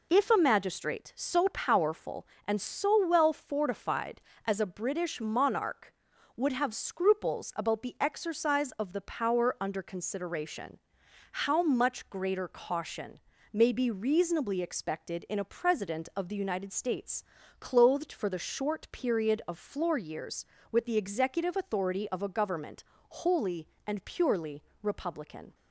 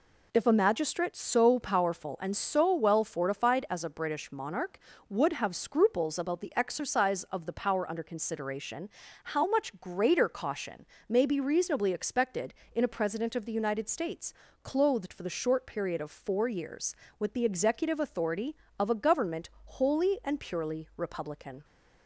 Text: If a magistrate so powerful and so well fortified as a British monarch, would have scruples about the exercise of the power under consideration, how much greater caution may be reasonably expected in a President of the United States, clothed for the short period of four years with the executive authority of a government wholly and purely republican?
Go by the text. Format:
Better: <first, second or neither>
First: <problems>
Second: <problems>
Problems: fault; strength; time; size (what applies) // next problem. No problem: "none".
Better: second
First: pauses between "caution" and "may"; slight; at 13.1 s; 0.34 s long // says "floor" for "four"; at 19.5 s // pauses between "government" and "wholly"; slight; at 22.8 s; 0.26 s long // pauses between "purely" and "republican"; slight; at 24.6 s; 0.22 s long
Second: pauses between "caution" and "may"; slight; at 10.8 s; 0.22 s long